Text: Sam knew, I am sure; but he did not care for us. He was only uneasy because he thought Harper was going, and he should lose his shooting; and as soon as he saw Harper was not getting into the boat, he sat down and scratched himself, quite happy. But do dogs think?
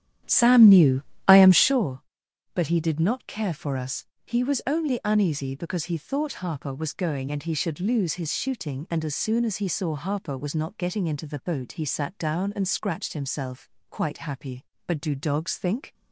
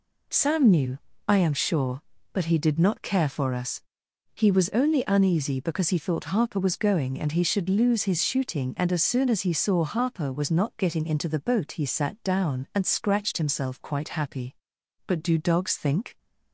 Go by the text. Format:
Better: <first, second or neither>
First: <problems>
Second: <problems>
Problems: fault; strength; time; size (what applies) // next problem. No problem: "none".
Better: second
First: starts louder than the rest; strong; until 1.9 s; 10.5 dB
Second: none